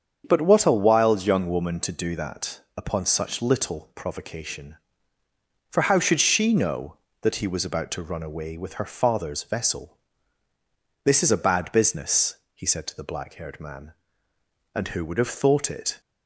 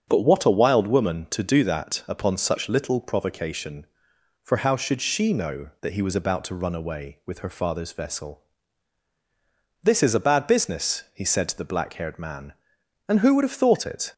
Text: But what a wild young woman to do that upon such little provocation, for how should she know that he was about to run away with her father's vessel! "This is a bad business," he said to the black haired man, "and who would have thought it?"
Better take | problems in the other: first | starts louder than the rest; until 1.0 s; 7 dB; strong in the first // skips "young"; at 0.8 s

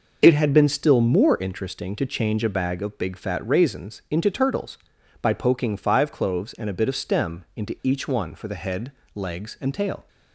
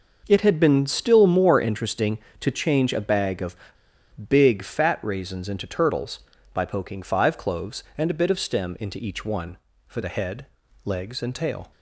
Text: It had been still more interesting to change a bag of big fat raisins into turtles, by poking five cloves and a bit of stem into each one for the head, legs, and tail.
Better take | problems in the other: first | pauses between "of" and "big"; noticeable; at 3.5 s; 0.74 s long

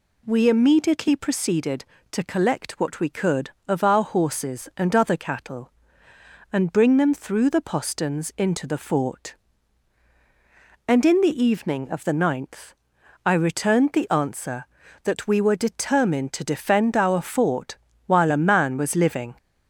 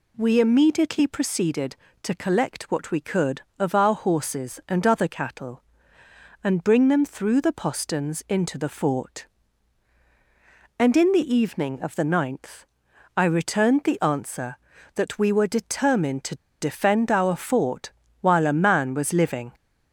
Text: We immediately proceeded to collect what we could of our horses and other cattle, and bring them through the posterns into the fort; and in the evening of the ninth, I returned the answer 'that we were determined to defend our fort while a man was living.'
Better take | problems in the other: first | pauses between "to" and "defend"; slight; at 16.3 s; 0.24 s long // pauses between "fort" and "while"; slight; at 17.8 s; 0.32 s long; slight in the first

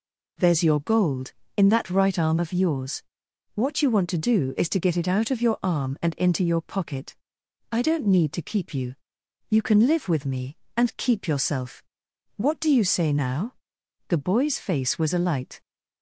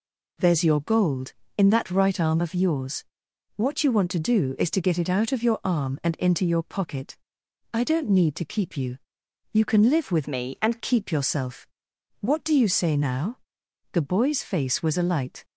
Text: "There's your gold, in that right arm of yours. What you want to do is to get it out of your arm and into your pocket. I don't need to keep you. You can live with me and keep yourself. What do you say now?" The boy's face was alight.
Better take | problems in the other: first | changes voice from "me" to "and"; from 10.2 to 10.7 s; 0.5 s long

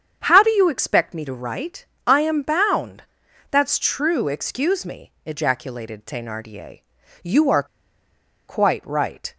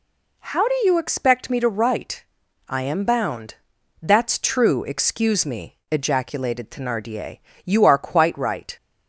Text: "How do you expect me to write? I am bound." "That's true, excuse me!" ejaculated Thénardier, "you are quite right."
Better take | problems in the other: second | starts louder than the rest; strong; until 1.2 s; 8 dB // pauses between "are" and "quite"; noticeable; at 7.6 s; 0.84 s long

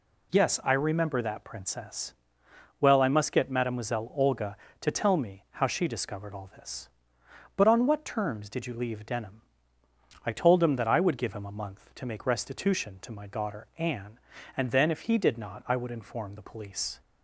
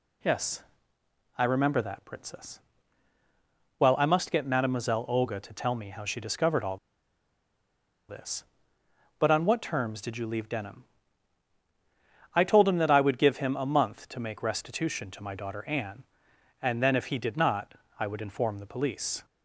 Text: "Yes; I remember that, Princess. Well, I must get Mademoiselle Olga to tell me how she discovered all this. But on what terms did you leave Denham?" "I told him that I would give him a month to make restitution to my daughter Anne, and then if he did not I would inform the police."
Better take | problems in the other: first | pauses between "all" and "this"; strong; at 6.7 s; 1.3 s long // pauses between "not" and "I"; slight; at 17.7 s; 0.24 s long

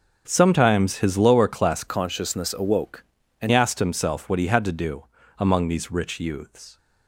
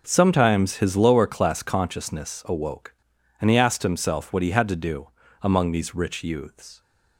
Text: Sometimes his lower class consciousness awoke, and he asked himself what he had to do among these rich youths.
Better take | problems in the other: second | starts louder than the rest; until 1.2 s; 7 dB // changes voice from "consciousness" to "and"; from 1.8 to 3.5 s; 1.7 s long // pauses between "do" and "among"; slight; at 5.0 s; 0.34 s long; slight in the second

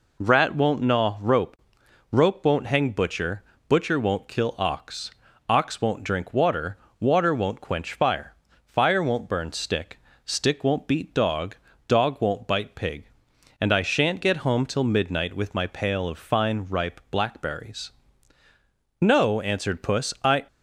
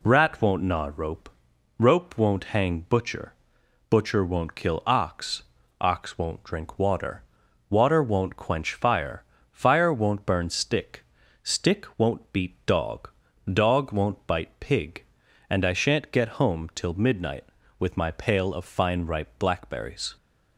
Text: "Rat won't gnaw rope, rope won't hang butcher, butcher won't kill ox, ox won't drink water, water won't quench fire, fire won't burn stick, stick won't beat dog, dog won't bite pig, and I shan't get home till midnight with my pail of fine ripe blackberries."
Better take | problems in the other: second | goes on to say "No answered puss I"; from 19.0 s on; 1.4 s long

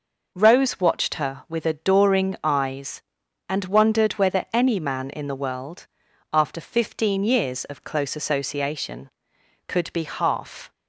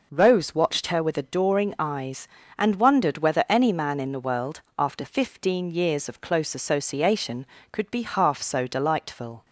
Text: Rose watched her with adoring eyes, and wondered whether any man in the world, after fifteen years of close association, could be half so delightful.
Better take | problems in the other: second | stops before "so delightful"; at 10.7 s

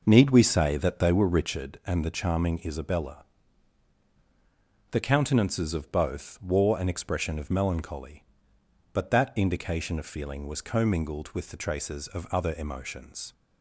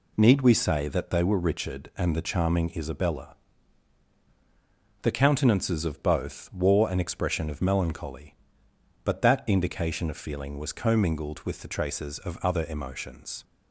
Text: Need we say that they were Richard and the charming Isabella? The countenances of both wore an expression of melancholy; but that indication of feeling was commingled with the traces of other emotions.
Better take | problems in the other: second | starts louder than the rest; noticeable; until 1.7 s; 5.5 dB

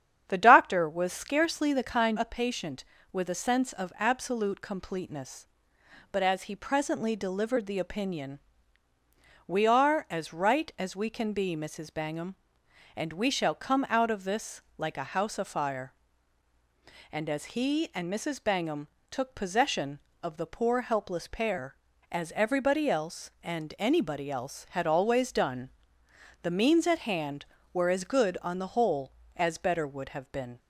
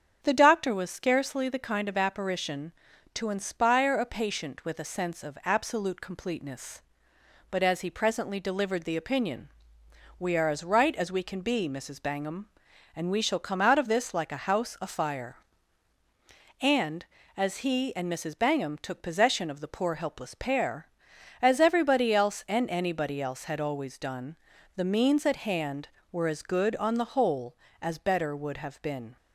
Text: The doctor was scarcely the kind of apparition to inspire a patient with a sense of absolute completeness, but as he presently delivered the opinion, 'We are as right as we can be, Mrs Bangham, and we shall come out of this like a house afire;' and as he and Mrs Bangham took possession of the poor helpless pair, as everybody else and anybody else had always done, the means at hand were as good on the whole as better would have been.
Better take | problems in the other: second | starts louder than the rest; strong; until 1.2 s; 9 dB; strong in the second // skips "of apparition to inspire"; at 2.1 s // pauses between "this" and "like"; slight; at 14.6 s; 0.16 s long // pauses between "Bangham" and "took"; slight; at 18.8 s; 0.20 s long

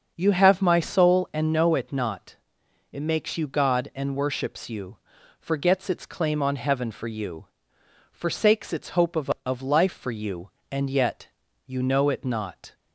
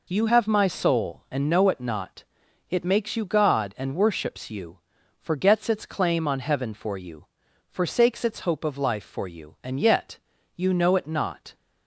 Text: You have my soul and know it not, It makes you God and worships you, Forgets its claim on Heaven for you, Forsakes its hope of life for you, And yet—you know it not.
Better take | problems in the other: second | starts louder than the rest; until 1.1 s; 6.5 dB // says "of" twice; at 9.4 s

